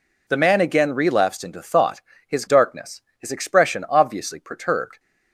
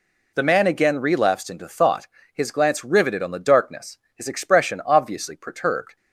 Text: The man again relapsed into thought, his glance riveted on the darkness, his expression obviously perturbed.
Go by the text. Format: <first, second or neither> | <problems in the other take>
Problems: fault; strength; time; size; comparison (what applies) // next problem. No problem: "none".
second | skips "glance riveted on the"; at 2.4 s